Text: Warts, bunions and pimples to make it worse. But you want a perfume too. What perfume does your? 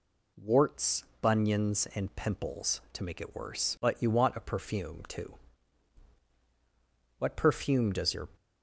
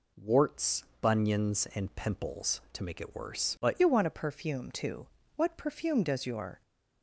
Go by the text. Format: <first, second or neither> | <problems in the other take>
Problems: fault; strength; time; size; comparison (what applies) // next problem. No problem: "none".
first | changes voice at "you"; from 3.7 s on; 2.9 s long